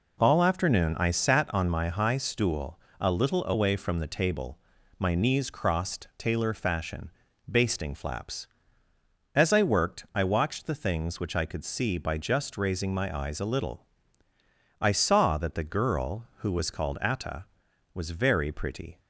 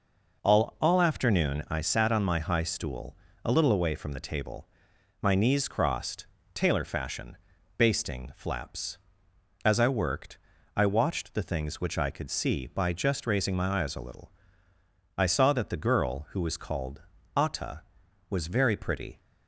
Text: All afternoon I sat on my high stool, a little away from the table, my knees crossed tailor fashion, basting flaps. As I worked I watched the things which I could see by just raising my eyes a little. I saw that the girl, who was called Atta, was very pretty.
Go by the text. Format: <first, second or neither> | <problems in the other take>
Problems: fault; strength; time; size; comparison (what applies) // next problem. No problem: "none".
first | says "All" twice; at 0.7 s // pauses between "crossed" and "tailor"; slight; at 6.2 s; 0.26 s long // pauses between "worked" and "I"; at 10.3 s; 0.40 s long // pauses between "called" and "Atta"; slight; at 17.0 s; 0.34 s long